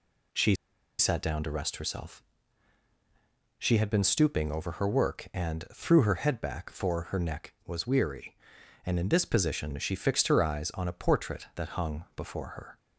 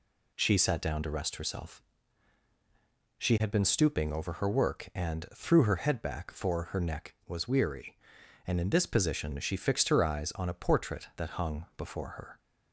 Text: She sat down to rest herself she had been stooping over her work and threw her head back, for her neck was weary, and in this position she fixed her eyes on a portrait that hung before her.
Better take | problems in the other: second | pauses between "She" and "sat"; at 0.5 s; 0.44 s long // pauses between "herself" and "she"; strong; at 2.2 s; 1.3 s long; strong in the second

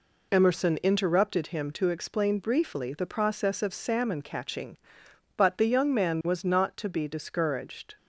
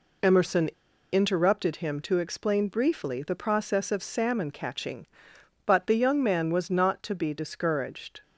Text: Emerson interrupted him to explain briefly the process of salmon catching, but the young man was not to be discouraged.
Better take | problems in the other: first | pauses between "Emerson" and "interrupted"; at 0.6 s; 0.42 s long

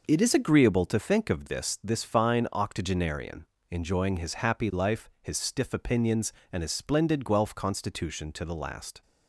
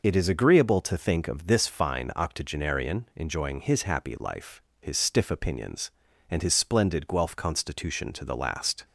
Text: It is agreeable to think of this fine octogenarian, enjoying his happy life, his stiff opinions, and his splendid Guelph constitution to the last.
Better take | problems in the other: second | says "this" twice; at 1.8 s

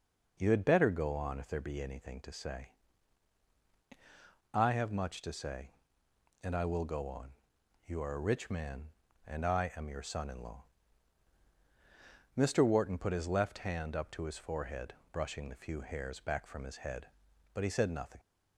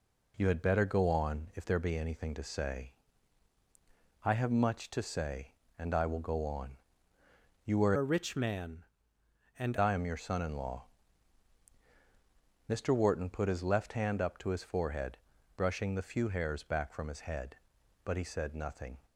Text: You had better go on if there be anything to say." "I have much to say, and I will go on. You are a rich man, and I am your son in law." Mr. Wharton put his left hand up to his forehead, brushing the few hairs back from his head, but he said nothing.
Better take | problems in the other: first | changes voice from "a" to "and"; from 7.9 to 9.7 s; 1.8 s long

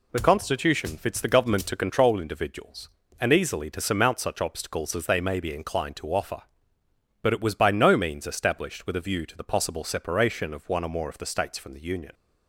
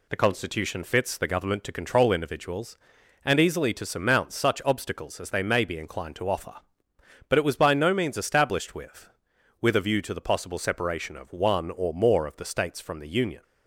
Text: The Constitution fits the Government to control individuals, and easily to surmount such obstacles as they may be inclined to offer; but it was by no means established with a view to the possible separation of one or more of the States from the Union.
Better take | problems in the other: first | says "with" twice; at 9.6 s

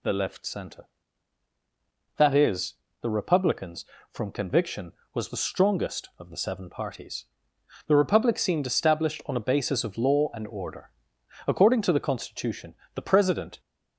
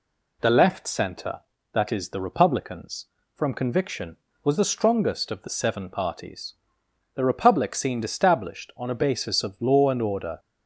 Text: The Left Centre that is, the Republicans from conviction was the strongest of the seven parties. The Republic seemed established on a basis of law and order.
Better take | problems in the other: second | goes on to say "According to the constitution the president"; strong; from 11.4 s on; 2.1 s long

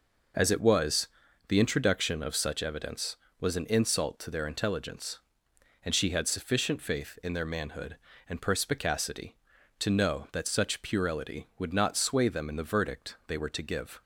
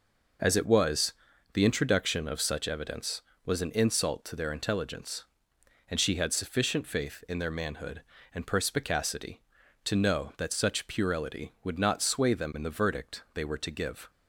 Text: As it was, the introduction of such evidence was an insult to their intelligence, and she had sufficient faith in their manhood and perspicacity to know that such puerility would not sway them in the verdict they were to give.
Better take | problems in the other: neither | none

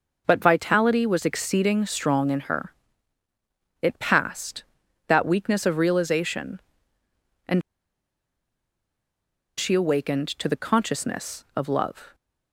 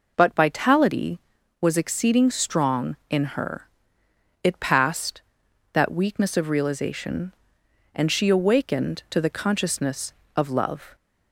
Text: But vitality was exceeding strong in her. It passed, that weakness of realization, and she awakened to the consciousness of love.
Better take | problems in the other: second | pauses between "and" and "she"; strong; at 7.6 s; 1.9 s long

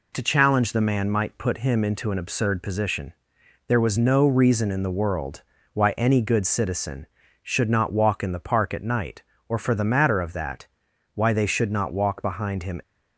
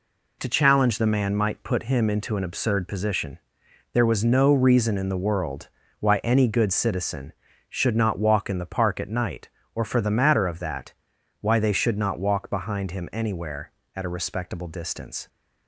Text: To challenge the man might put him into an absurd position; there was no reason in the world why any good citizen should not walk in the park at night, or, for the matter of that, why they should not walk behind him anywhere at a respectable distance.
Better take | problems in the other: second | pauses between "world" and "why"; slight; at 5.4 s; 0.30 s long; slight in the second // stops before "anywhere at a respectable distance"; at 12.8 s

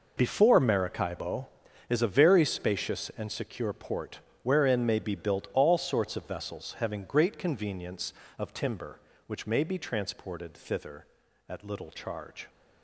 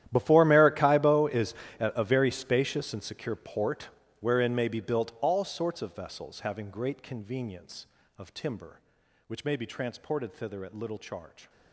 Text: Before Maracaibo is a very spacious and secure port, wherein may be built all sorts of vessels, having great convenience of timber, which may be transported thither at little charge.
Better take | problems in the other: first | gets quieter; strong; throughout; 18.5 dB // pauses between "is" and "a"; slight; at 1.5 s; 0.26 s long

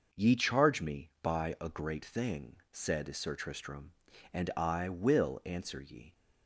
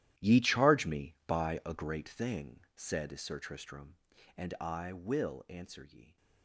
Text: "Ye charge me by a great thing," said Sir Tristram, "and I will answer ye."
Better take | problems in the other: first | gets quieter; strong; throughout; 15.5 dB

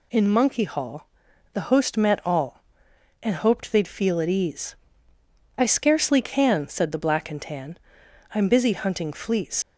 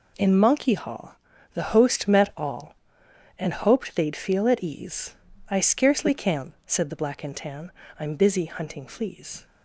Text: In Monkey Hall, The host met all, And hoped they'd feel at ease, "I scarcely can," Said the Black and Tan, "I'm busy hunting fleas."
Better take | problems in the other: second | leaves "fleas" unfinished; at 9.6 s; 70 ms

